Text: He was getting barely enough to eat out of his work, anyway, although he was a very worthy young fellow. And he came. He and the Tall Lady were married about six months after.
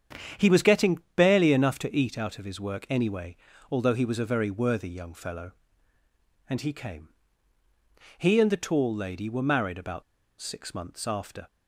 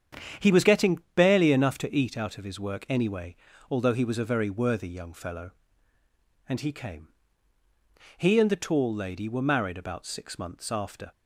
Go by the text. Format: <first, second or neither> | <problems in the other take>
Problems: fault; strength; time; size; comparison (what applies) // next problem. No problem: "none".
second | starts louder than the rest; strong; until 1.5 s; 9 dB; strong in the second // pauses between "getting" and "barely"; slight; at 0.9 s; 0.16 s long; slight in the second // pauses between "about" and "six"; at 10.0 s; 0.37 s long